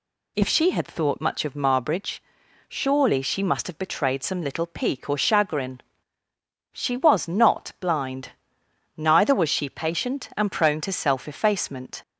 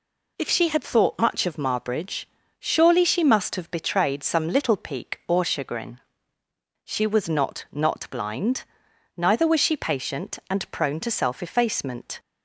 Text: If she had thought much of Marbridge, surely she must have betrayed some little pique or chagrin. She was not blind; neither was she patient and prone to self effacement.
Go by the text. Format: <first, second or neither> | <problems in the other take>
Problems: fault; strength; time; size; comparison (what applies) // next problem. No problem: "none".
first | says "not" twice; at 7.7 s